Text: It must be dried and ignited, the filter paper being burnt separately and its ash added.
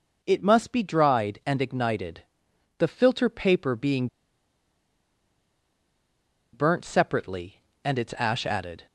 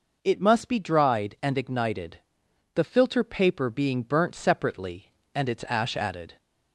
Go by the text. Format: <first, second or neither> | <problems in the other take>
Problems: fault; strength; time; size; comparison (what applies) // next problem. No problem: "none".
second | pauses between "being" and "burnt"; strong; at 4.0 s; 2.4 s long